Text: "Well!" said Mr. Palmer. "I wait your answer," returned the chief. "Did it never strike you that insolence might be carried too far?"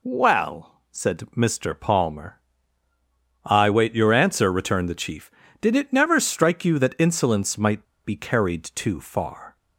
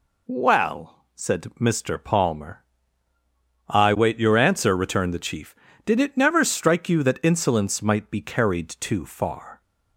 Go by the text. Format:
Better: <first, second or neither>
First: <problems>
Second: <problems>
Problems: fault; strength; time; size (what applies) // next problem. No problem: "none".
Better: second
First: pauses between "might" and "be"; slight; at 7.8 s; 0.20 s long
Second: none